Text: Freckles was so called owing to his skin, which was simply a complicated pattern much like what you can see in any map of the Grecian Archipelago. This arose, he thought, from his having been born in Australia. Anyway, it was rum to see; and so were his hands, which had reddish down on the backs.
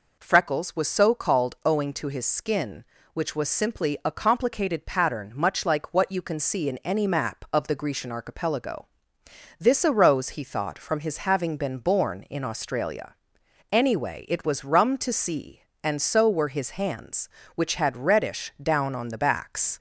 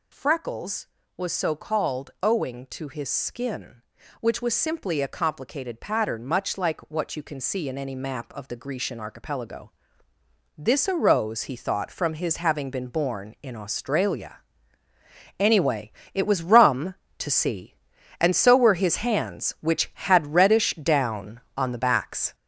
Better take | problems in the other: first | gets louder; noticeable; throughout; 6 dB

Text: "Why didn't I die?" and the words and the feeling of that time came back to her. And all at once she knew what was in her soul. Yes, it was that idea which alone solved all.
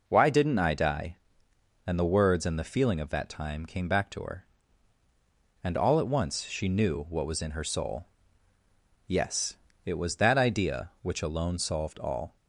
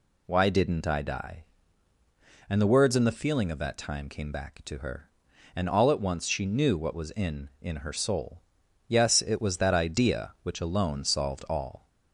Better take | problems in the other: first | says "in" twice; at 7.6 s

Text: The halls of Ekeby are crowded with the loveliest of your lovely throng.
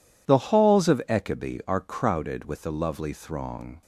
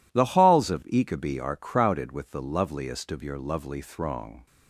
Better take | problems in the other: second | skips "loveliest of your"; at 2.7 s

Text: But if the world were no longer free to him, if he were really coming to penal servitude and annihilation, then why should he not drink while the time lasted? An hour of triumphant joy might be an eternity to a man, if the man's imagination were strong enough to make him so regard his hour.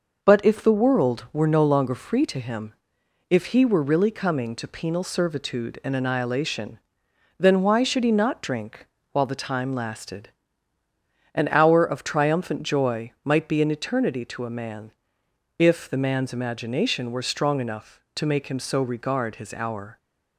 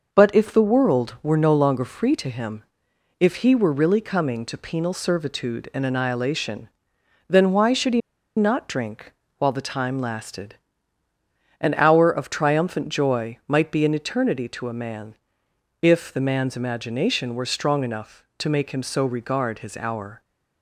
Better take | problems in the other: first | pauses between "he" and "not"; at 8.0 s; 0.36 s long // pauses between "drink" and "while"; slight; at 9.1 s; 0.26 s long; slight in the first

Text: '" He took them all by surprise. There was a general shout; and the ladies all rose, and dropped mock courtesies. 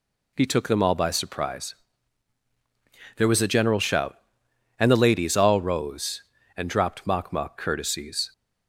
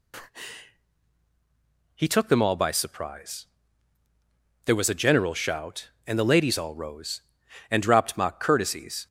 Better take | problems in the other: second | says "mock" twice; at 7.3 s

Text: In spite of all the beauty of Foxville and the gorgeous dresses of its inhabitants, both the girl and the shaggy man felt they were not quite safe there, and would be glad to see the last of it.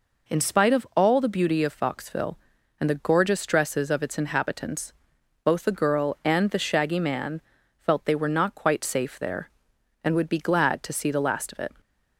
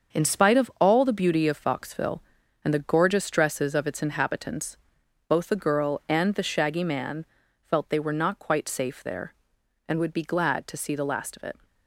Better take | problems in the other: first | gets quieter; strong; throughout; 8.5 dB // pauses between "man" and "felt"; at 7.2 s; 0.38 s long; also in the first

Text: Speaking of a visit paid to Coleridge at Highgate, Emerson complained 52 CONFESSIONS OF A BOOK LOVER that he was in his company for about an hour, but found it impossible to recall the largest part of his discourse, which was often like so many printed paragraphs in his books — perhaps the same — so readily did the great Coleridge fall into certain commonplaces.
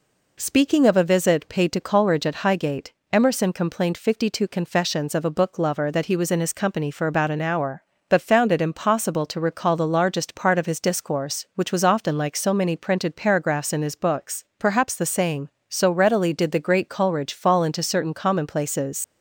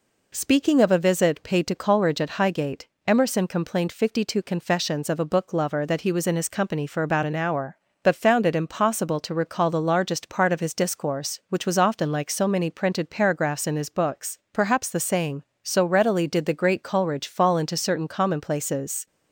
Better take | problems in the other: second | leaves "commonplaces" unfinished; at 19.0 s; 70 ms

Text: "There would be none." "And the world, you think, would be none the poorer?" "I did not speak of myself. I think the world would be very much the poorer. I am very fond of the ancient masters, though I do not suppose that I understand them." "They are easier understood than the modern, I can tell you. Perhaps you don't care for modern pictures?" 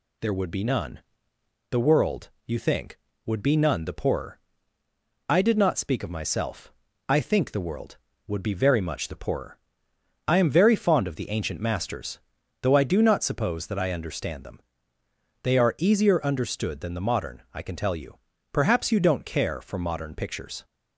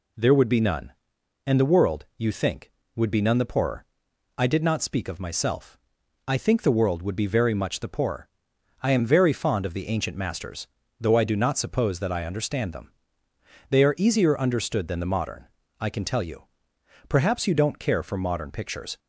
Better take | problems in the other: second | skips "And"; at 1.3 s

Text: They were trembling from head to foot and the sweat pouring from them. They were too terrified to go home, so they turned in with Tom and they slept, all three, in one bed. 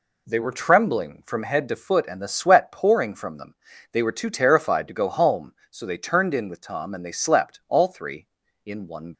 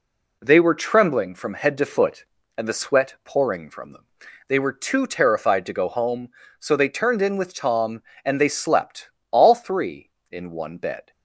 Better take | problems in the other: second | stops before "bed"; at 9.1 s

